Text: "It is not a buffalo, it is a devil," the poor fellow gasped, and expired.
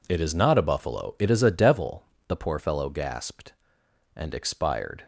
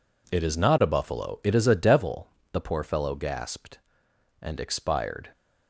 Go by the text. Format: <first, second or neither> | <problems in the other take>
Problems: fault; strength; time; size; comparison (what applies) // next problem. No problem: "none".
neither | none